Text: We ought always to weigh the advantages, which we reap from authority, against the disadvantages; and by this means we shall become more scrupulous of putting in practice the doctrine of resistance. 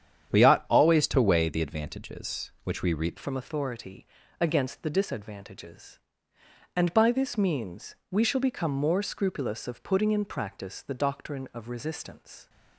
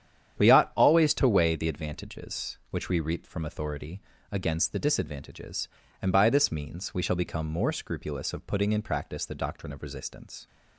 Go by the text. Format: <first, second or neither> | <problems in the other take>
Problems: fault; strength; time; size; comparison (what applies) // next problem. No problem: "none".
second | starts louder than the rest; strong; until 1.4 s; 9 dB; strong in the second // changes voice at "from"; from 3.1 s on; 9.3 s long // pauses between "means" and "we"; slight; at 7.9 s; 0.16 s long